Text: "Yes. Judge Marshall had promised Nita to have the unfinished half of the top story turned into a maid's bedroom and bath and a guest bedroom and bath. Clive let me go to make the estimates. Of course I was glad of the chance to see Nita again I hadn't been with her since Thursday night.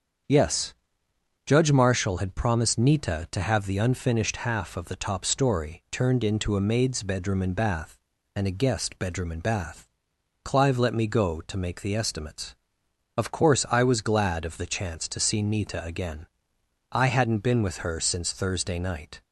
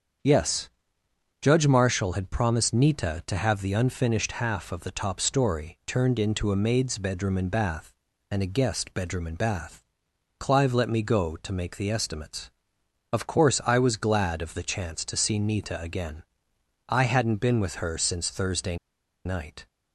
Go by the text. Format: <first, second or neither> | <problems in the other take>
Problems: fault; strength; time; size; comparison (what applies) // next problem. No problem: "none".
first | starts louder than the rest; strong; until 1.9 s; 7.5 dB; strong in the first // pauses between "again" and "I"; noticeable; at 16.2 s; 0.66 s long; noticeable in the first // pauses between "Thursday" and "night"; noticeable; at 18.7 s; 0.49 s long